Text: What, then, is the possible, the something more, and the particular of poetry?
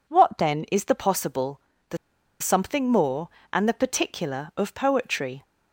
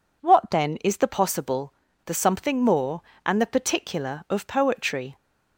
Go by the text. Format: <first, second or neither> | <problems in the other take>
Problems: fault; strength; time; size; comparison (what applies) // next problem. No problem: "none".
second | pauses between "the" and "something"; at 1.9 s; 0.43 s long